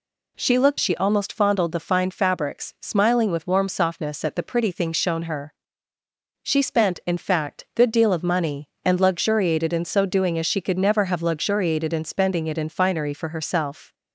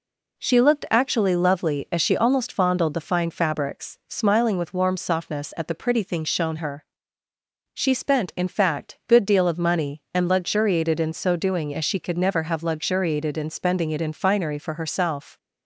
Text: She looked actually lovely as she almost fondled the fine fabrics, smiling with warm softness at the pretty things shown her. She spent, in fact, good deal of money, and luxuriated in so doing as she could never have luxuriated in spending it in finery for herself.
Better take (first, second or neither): second